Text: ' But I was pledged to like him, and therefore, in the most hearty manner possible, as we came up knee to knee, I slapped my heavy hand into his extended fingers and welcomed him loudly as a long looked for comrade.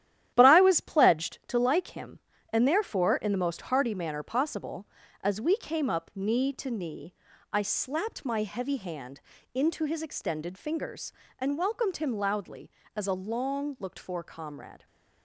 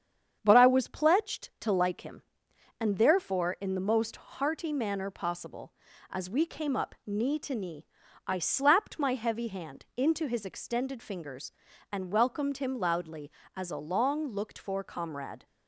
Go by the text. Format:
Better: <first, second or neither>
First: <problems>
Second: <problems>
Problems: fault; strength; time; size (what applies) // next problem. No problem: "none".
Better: second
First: gets quieter; strong; throughout; 8 dB // starts louder than the rest; strong; until 1.3 s; 11.5 dB // pauses between "hand" and "into"; slight; at 9.1 s; 0.34 s long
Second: starts louder than the rest; strong; until 1.4 s; 8.5 dB